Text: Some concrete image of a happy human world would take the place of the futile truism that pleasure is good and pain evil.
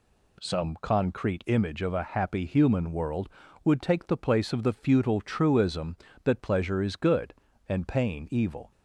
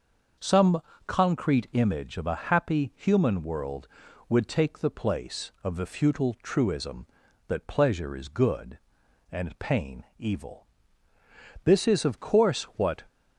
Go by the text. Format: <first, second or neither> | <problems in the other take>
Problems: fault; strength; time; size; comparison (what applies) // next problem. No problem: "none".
first | starts louder than the rest; until 1.6 s; 6 dB // pauses between "Some" and "concrete"; slight; at 0.8 s; 0.26 s long // goes on to say "This is of course what"; from 11.6 s on; 1.3 s long